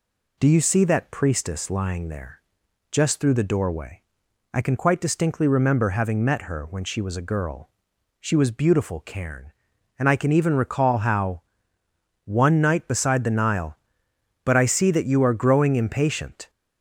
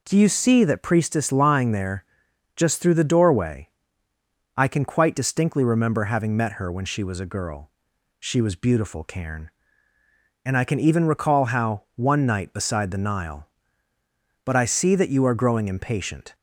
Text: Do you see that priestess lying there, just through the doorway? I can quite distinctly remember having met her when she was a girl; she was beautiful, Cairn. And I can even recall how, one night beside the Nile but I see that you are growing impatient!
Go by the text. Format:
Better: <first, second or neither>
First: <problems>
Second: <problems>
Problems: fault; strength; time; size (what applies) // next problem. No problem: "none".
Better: neither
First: none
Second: none